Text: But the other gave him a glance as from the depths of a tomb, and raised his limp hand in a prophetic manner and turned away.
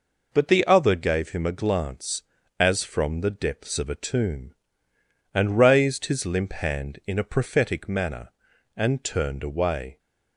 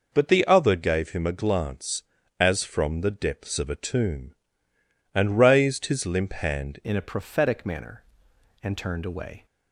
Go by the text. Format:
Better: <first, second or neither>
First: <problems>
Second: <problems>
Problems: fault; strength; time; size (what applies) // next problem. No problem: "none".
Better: first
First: none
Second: changes voice at "in"; from 6.8 s on; 2.6 s long